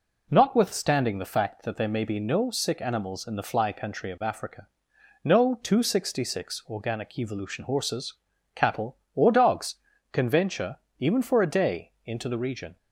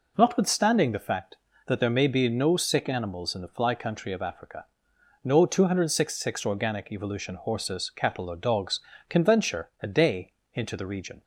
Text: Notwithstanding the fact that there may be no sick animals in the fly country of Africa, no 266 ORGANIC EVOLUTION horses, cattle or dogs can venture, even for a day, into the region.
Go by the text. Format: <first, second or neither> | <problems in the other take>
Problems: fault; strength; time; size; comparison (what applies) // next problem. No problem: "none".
first | skips "even for"; at 9.7 s